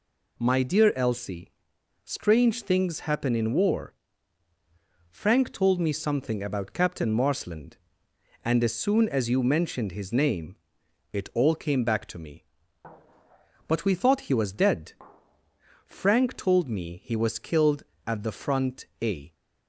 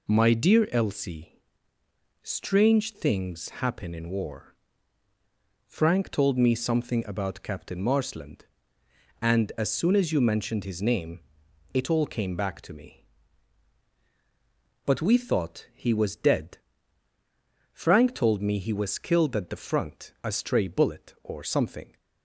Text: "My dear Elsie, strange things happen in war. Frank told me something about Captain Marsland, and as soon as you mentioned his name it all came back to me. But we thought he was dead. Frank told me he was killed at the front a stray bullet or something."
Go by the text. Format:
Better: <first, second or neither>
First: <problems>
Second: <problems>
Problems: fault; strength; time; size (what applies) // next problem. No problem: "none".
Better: second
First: pauses between "name" and "it"; noticeable; at 10.5 s; 0.56 s long // stops before "stray bullet or something"; at 19.3 s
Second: pauses between "name" and "it"; noticeable; at 11.1 s; 0.56 s long